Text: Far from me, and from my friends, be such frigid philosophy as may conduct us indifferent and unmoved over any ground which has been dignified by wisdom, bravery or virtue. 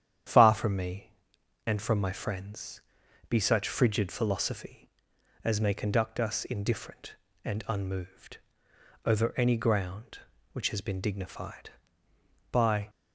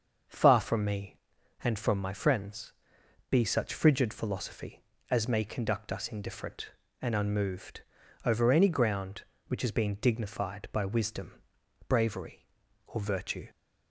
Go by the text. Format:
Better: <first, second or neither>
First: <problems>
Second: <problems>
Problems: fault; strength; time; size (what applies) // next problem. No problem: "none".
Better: second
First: starts louder than the rest; strong; until 1.8 s; 9.5 dB // pauses between "unmoved" and "over"; noticeable; at 8.3 s; 0.70 s long // stops before "wisdom bravery or virtue"; at 12.8 s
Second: starts louder than the rest; until 1.7 s; 6.5 dB // pauses between "unmoved" and "over"; at 7.8 s; 0.42 s long